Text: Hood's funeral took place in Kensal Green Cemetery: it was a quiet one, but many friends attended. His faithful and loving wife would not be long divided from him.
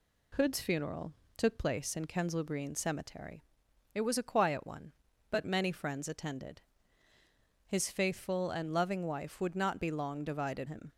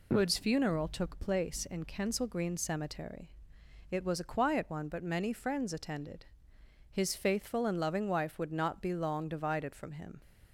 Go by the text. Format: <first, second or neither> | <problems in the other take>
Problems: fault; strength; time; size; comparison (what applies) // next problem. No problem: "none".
second | pauses between "funeral" and "took"; slight; at 1.1 s; 0.24 s long // skips "from"; at 10.6 s